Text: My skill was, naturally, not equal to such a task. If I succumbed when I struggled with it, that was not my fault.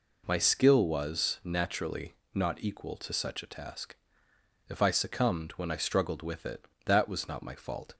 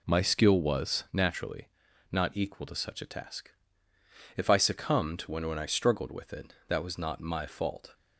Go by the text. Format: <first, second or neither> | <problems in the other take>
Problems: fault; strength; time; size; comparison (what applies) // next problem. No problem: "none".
first | says "when" twice; at 5.4 s